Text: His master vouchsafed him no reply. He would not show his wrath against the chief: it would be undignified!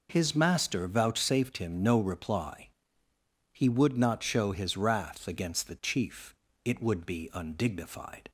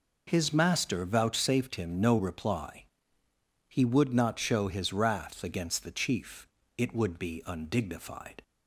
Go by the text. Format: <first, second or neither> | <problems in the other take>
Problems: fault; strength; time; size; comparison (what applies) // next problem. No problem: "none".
neither | none